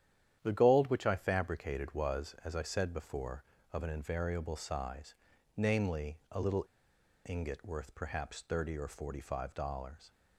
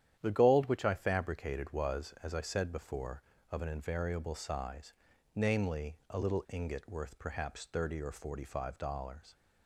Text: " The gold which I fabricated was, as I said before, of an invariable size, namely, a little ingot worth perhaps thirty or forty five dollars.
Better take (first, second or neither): second